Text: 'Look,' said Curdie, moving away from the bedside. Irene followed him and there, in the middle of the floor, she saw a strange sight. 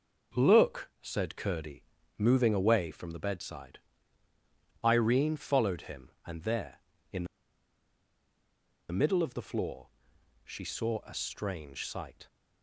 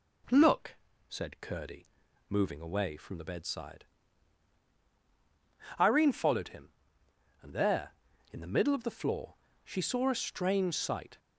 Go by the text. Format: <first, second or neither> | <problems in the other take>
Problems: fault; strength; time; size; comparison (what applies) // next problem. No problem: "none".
second | pauses between "in" and "the"; strong; at 7.2 s; 1.6 s long